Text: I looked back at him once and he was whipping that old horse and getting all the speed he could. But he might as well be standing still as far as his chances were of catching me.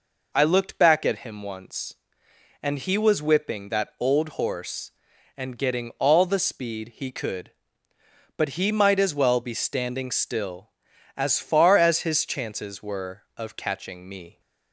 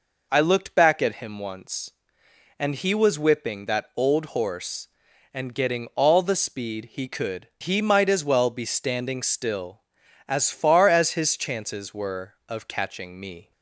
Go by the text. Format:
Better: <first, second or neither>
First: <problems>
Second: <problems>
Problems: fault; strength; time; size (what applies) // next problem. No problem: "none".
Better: first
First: none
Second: skips "But"; at 7.5 s